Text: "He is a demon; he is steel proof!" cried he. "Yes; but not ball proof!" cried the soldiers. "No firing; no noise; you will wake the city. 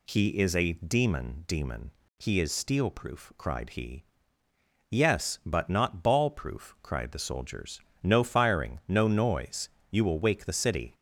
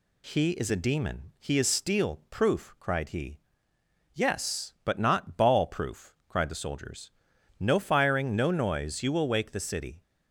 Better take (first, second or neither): second